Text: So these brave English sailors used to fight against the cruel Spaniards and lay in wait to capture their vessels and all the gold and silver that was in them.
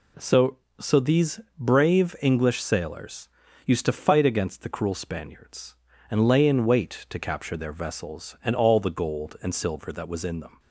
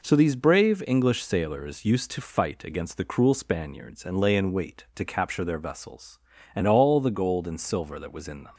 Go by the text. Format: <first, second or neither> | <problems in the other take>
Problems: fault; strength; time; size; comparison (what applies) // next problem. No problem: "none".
second | says "So" twice; at 0.7 s // pauses between "these" and "brave"; slight; at 1.3 s; 0.18 s long // pauses between "sailors" and "used"; slight; at 3.2 s; 0.36 s long